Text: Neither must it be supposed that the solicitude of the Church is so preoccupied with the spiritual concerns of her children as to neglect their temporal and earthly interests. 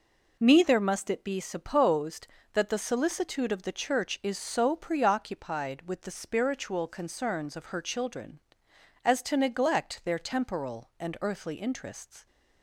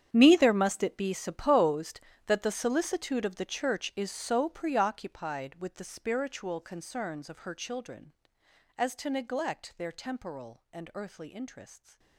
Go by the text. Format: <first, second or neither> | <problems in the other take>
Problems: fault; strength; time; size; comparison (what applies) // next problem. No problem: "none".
first | gets quieter; strong; throughout; 16.5 dB